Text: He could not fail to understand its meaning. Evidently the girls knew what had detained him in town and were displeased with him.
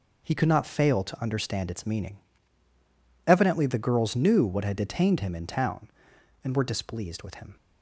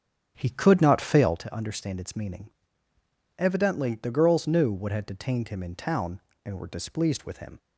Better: first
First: none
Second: starts louder than the rest; strong; until 1.4 s; 9 dB

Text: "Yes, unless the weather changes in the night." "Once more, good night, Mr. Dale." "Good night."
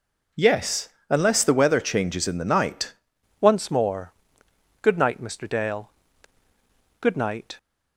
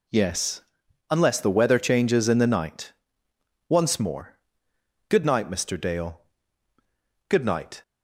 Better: second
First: changes voice at "Once"; from 3.4 s on; 4.1 s long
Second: none

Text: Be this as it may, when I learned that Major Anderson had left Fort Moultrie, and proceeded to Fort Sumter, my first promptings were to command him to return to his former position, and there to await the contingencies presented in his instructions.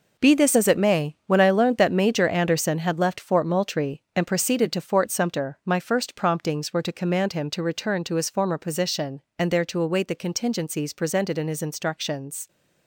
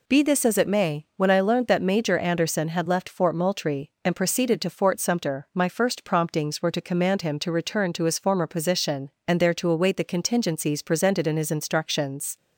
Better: second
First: gets quieter; strong; throughout; 8.5 dB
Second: none

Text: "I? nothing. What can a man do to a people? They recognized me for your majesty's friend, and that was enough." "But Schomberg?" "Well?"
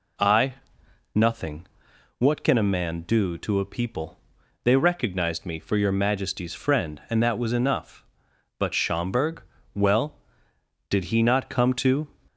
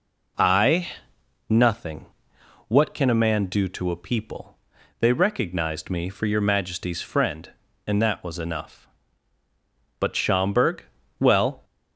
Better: second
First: goes on to say "Did he not come to"; noticeable; from 10.8 s on; 1.2 s long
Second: none

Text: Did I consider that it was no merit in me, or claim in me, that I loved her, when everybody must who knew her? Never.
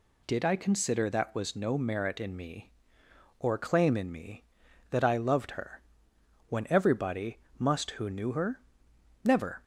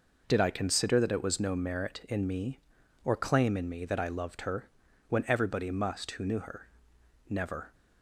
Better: second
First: skips "it"; at 1.3 s // pauses between "everybody" and "must"; slight; at 7.3 s; 0.20 s long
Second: none

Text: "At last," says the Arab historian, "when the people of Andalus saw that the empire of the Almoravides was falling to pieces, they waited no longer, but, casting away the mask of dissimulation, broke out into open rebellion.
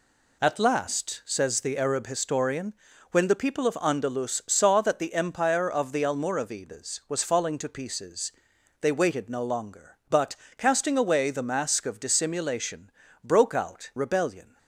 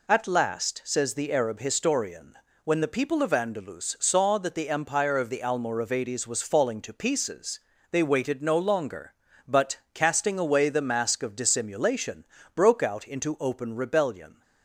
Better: second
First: skips "into open"; at 13.9 s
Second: none

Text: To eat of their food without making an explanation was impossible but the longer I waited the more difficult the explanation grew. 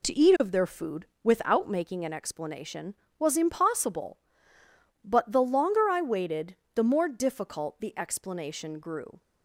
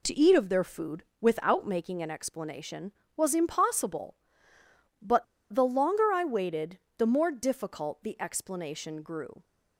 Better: first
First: pauses between "food" and "without"; slight; at 1.0 s; 0.18 s long // pauses between "waited" and "the"; slight; at 6.5 s; 0.20 s long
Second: pauses between "food" and "without"; slight; at 1.0 s; 0.18 s long // pauses between "but" and "the"; slight; at 5.2 s; 0.28 s long // pauses between "waited" and "the"; slight; at 6.7 s; 0.20 s long

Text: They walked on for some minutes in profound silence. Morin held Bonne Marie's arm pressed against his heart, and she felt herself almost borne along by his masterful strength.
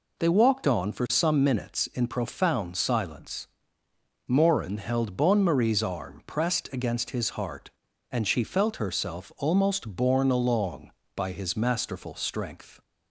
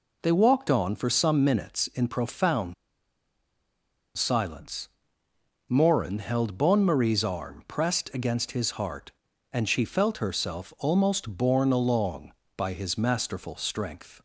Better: first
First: none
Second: pauses between "profound" and "silence"; strong; at 2.7 s; 1.4 s long

